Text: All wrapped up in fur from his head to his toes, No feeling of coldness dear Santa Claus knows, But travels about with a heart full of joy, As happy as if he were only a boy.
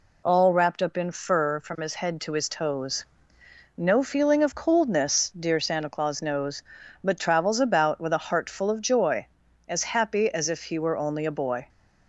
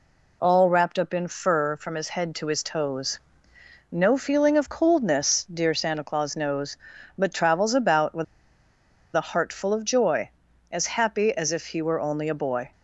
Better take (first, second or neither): first